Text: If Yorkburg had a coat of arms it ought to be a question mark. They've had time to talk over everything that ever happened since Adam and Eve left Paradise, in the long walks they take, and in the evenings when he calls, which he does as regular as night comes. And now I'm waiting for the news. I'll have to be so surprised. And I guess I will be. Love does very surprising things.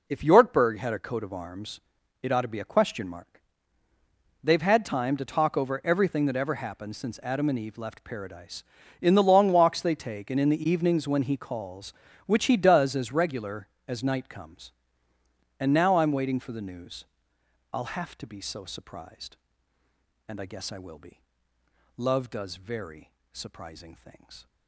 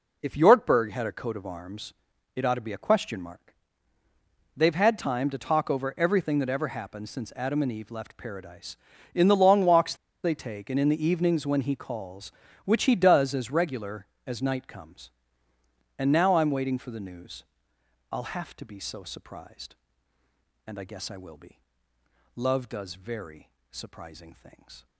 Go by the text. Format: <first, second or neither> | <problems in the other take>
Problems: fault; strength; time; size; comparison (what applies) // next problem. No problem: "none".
first | pauses between "arms" and "it"; at 1.9 s; 0.44 s long; also in the first // pauses between "walks" and "they"; slight; at 9.9 s; 0.29 s long // pauses between "very" and "surprising"; slight; at 23.4 s; 0.22 s long; slight in the first